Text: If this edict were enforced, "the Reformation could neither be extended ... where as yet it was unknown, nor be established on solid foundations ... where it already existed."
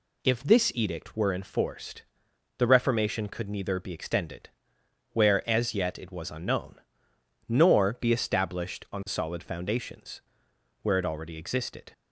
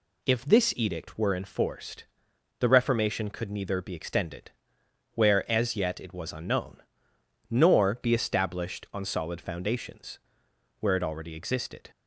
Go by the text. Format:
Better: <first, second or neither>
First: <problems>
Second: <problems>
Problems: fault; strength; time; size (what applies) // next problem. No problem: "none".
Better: neither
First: none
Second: none